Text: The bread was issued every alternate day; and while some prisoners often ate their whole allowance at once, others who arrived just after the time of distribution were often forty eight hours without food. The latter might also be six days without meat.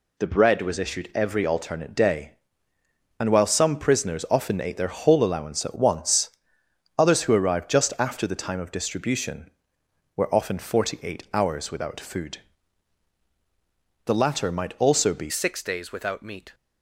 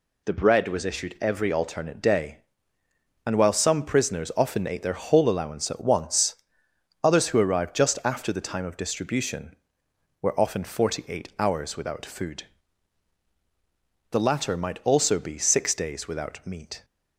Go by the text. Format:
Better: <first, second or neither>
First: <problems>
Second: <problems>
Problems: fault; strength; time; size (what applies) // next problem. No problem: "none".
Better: second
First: changes voice at "six"; from 15.2 s on; 1.3 s long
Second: none